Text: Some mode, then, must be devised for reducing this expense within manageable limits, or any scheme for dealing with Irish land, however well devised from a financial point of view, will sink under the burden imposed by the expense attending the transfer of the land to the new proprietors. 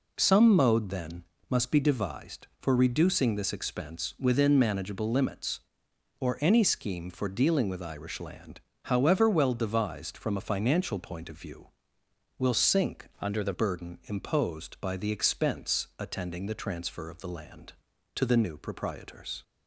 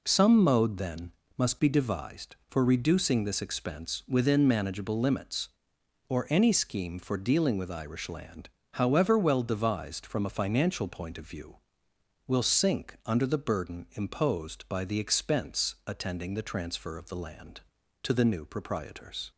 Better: second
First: changes voice from "under" to "the"; from 13.2 to 13.5 s; 0.3 s long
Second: none

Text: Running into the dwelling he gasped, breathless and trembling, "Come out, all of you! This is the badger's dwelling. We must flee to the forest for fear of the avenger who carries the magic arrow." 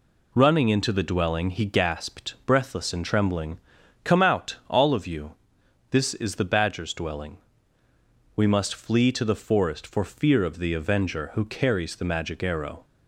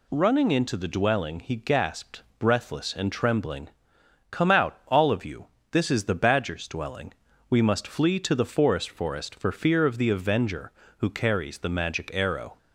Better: first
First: none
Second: says "forest" twice; at 8.8 s

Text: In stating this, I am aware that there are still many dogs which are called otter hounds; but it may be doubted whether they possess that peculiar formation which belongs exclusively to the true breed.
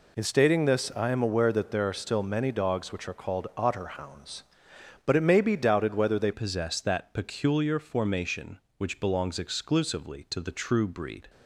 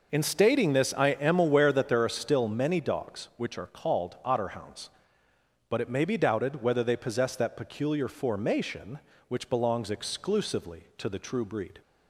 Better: second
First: changes voice at "possess"; from 6.3 s on; 4.9 s long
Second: none

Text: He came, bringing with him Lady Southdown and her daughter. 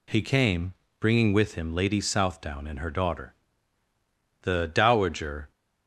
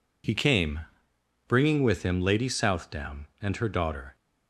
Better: second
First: goes on to say "The dowager"; noticeable; from 4.4 s on; 1.1 s long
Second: none

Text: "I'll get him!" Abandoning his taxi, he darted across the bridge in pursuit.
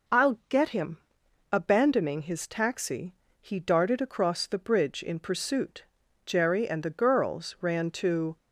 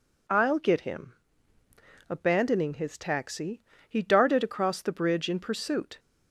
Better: second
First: goes on to say "Jerry and the girls ran to"; strong; from 6.2 s on; 2.1 s long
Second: none

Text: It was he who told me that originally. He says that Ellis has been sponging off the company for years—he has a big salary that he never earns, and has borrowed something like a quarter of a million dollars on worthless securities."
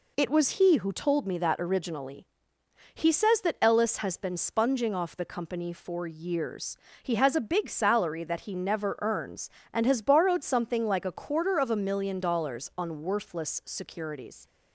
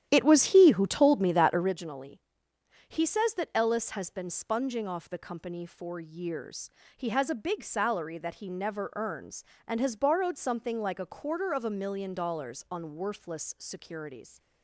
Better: first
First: none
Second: starts louder than the rest; strong; until 1.7 s; 11 dB

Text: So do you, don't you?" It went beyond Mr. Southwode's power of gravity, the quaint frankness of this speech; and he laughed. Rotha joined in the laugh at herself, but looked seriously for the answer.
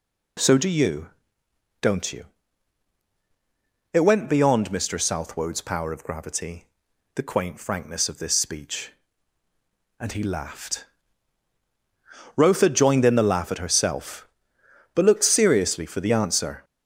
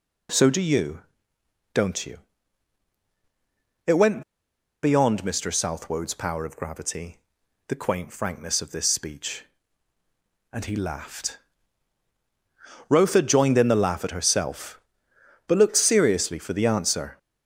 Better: first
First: none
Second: pauses between "went" and "beyond"; noticeable; at 4.2 s; 0.60 s long

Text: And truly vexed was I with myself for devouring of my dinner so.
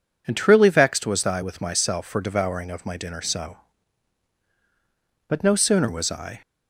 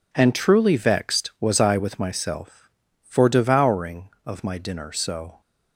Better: second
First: goes on to say "But no sooner was I"; noticeable; from 5.2 s on; 1.1 s long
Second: none

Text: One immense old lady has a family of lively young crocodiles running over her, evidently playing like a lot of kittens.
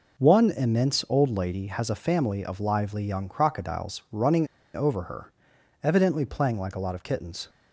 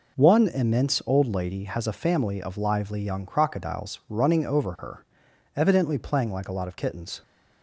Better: second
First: pauses between "running" and "over"; slight; at 4.4 s; 0.28 s long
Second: none

